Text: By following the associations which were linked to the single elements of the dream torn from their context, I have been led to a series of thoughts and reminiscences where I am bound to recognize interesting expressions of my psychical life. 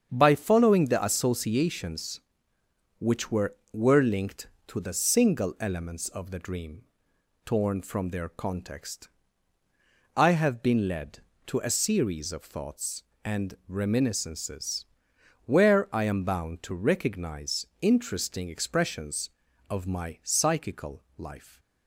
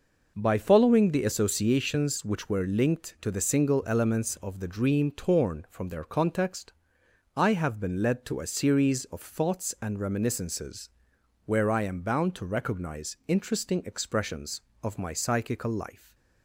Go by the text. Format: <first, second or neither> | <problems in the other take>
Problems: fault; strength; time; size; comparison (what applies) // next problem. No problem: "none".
second | starts louder than the rest; strong; until 1.1 s; 7.5 dB // says "were" twice; at 3.7 s // pauses between "dream" and "torn"; noticeable; at 6.8 s; 0.60 s long // pauses between "reminiscences" and "where"; noticeable; at 14.8 s; 0.58 s long; noticeable in the second // pauses between "recognize" and "interesting"; slight; at 17.6 s; 0.16 s long